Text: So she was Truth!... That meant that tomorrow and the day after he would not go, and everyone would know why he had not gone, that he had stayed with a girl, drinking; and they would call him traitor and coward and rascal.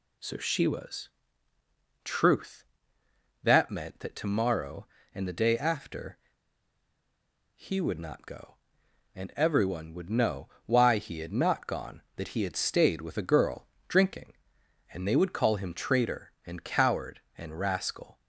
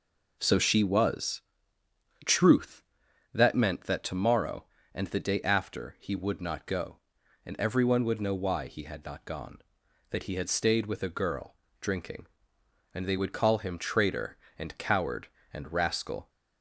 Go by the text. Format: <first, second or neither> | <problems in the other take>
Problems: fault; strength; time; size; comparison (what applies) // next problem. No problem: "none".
second | pauses between "was" and "Truth"; noticeable; at 1.0 s; 0.96 s long; noticeable in the second // pauses between "after" and "he"; strong; at 6.1 s; 1.3 s long // pauses between "know" and "why"; slight; at 10.4 s; 0.18 s long